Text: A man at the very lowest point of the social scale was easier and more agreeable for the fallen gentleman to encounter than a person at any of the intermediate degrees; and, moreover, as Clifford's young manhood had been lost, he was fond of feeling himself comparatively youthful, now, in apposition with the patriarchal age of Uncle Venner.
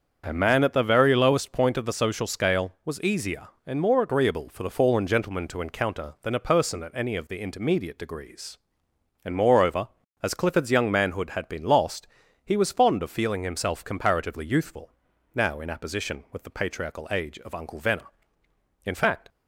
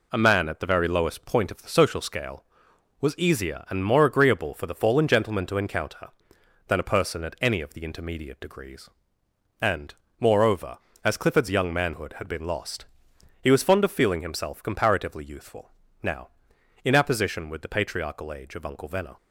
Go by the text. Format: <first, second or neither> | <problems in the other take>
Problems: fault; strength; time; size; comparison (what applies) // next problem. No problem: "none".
second | starts louder than the rest; until 1.2 s; 7 dB // goes on to say "In fact"; slight; from 18.8 s on; 0.44 s long